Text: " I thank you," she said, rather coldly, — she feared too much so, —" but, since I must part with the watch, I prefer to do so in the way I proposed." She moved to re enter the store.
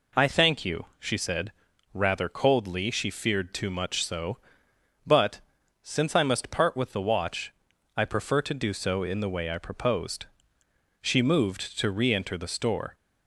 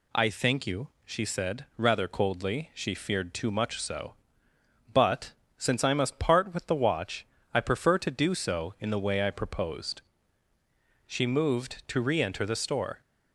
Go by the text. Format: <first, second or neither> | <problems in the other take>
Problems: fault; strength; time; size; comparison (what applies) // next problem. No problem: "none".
neither | none